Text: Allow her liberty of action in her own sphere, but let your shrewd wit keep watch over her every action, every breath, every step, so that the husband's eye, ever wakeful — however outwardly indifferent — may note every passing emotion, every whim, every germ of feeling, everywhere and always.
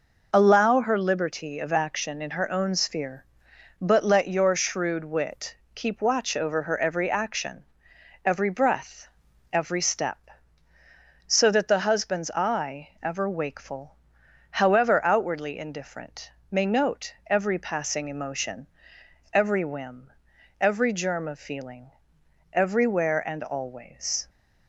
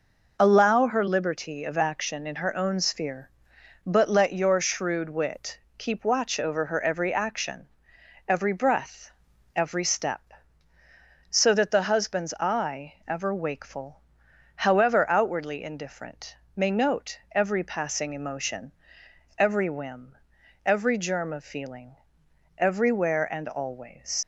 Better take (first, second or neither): first